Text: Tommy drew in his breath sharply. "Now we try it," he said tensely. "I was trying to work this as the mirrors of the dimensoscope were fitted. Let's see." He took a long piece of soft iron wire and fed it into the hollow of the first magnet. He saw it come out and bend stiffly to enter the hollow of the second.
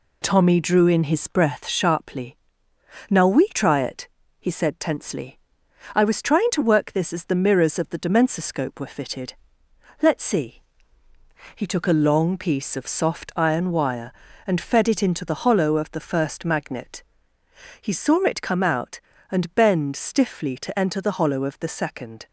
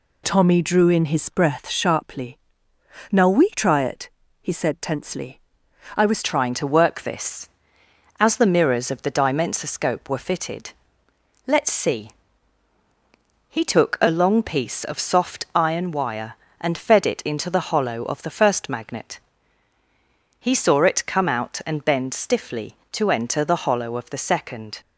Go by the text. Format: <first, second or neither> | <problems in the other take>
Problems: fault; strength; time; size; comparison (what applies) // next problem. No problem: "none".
first | changes voice at "trying"; from 6.2 s on; 18.6 s long